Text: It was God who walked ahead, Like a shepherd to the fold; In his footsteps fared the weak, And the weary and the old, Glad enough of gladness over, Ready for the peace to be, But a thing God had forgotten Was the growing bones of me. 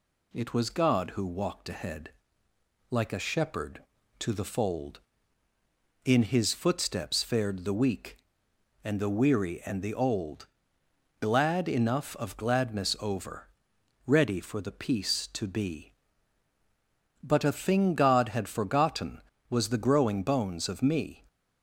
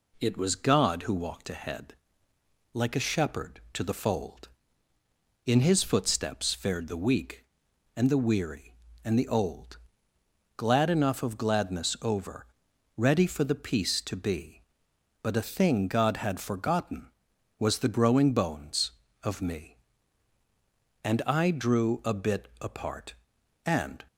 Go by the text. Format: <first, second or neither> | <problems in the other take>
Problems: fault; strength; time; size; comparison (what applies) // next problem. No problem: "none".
first | goes on to say "And I drew a bit apart And"; strong; from 21.0 s on; 3.0 s long